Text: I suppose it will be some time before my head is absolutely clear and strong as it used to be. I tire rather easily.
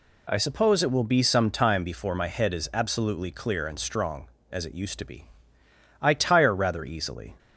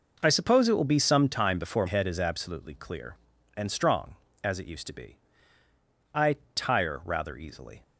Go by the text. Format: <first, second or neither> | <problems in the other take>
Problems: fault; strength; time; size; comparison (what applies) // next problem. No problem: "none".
first | skips "my"; at 1.8 s // pauses between "I" and "tire"; slight; at 6.3 s; 0.18 s long